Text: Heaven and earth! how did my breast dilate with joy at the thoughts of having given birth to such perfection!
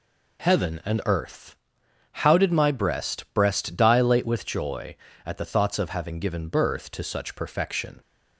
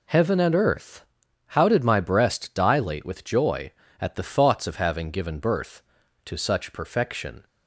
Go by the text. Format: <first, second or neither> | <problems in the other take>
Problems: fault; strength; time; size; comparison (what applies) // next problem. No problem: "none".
second | says "breast" twice; at 3.3 s